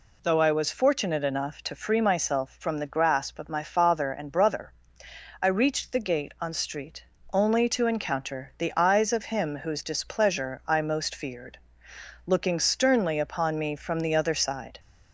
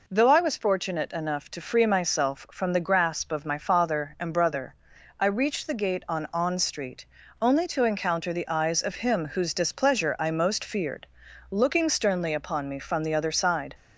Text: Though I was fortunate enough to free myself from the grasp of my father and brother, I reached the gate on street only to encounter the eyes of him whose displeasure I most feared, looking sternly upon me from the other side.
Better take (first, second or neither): first